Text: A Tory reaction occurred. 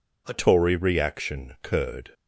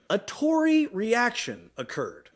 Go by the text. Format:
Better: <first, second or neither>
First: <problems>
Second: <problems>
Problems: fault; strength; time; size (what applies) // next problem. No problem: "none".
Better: second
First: changes voice at "Tory"; from 0.3 s on; 1.8 s long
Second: none